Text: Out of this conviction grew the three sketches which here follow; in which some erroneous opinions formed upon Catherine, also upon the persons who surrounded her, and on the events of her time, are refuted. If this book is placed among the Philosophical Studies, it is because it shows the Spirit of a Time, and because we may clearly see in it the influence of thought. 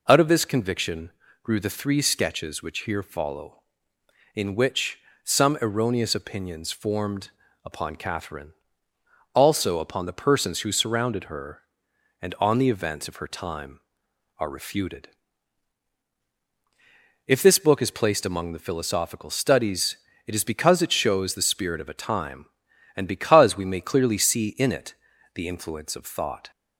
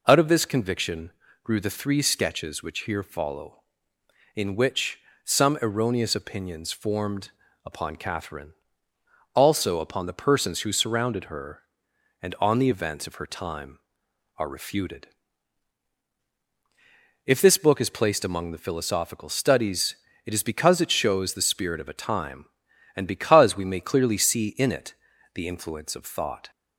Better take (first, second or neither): neither